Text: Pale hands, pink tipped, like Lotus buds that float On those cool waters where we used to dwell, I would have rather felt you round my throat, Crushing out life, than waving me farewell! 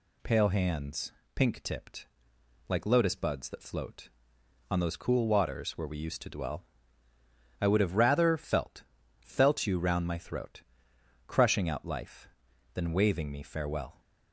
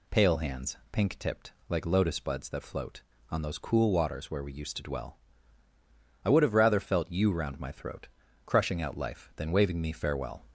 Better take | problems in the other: second | says "felt" twice; at 9.1 s

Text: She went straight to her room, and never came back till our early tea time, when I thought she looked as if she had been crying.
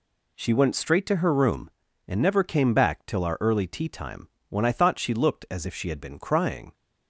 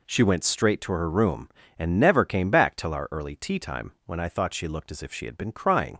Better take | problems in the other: neither | none

